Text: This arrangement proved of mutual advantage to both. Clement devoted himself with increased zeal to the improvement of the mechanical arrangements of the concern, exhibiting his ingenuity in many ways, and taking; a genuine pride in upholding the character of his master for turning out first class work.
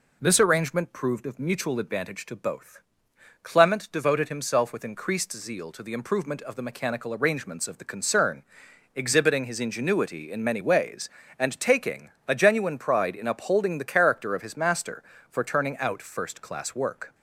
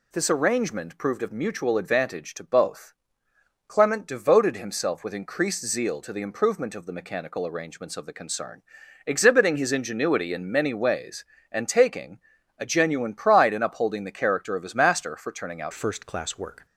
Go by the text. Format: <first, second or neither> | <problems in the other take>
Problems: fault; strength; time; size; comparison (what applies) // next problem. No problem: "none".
first | changes voice at "first"; from 15.7 s on; 0.9 s long